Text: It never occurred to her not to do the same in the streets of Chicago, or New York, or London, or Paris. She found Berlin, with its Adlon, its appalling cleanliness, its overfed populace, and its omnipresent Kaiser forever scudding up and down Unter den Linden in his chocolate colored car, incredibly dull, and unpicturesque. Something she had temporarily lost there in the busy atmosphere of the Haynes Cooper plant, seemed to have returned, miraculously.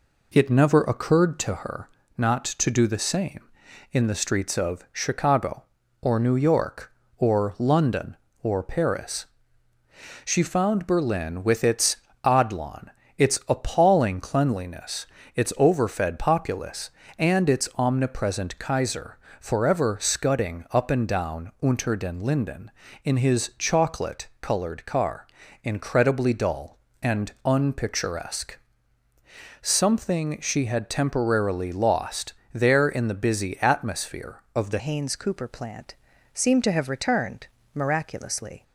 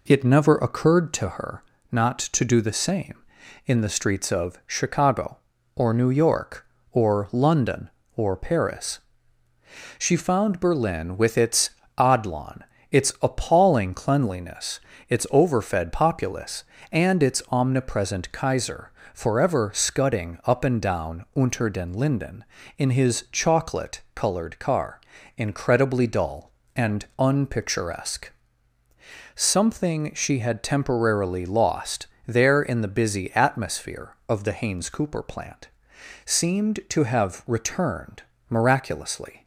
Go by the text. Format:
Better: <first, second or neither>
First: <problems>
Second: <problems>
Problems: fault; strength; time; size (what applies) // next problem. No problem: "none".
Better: second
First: pauses between "her" and "not"; slight; at 1.8 s; 0.28 s long // pauses between "its" and "Adlon"; slight; at 11.9 s; 0.28 s long // pauses between "Kaiser" and "forever"; slight; at 19.1 s; 0.20 s long // pauses between "lost" and "there"; slight; at 32.3 s; 0.20 s long // changes voice at "Haynes"; from 34.7 s on; 3.9 s long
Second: pauses between "her" and "not"; slight; at 1.6 s; 0.28 s long // pauses between "its" and "Adlon"; slight; at 11.6 s; 0.28 s long // pauses between "Kaiser" and "forever"; slight; at 18.9 s; 0.20 s long // pauses between "lost" and "there"; slight; at 32.0 s; 0.20 s long